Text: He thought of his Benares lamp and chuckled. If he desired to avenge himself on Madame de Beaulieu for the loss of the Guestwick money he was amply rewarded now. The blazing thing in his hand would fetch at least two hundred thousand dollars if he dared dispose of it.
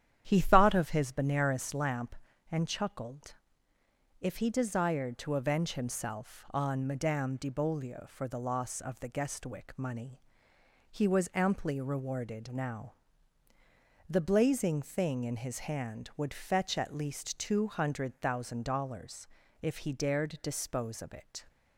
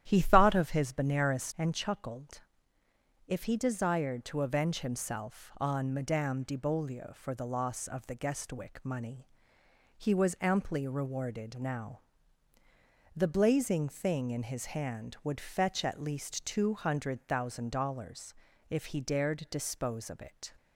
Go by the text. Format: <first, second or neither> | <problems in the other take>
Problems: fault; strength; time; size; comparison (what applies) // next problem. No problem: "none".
first | starts louder than the rest; strong; until 1.0 s; 11 dB; strong in the first // skips "lamp"; at 1.5 s // pauses between "money" and "he"; noticeable; at 9.2 s; 0.70 s long; noticeable in the first // pauses between "dollars" and "if"; slight; at 18.3 s; 0.34 s long; slight in the first